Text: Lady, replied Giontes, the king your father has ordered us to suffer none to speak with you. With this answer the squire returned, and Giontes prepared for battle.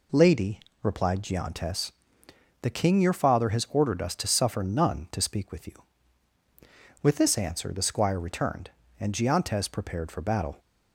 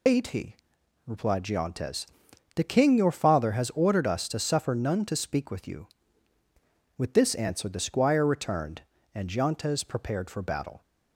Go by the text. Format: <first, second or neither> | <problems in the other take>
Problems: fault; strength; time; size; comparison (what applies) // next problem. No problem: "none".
first | loses the start of "Lady"; at 0.0 s; 125 ms